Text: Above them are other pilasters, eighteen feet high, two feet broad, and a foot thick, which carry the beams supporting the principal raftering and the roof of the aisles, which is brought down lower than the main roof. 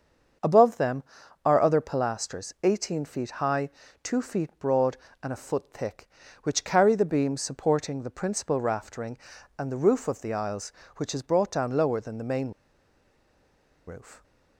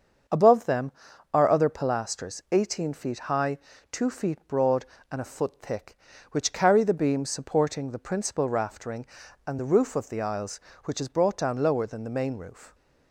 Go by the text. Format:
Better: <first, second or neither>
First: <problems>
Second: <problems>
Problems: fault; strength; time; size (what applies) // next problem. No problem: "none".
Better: second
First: starts louder than the rest; until 1.8 s; 7 dB // pauses between "main" and "roof"; strong; at 12.5 s; 1.3 s long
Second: starts louder than the rest; until 1.7 s; 7 dB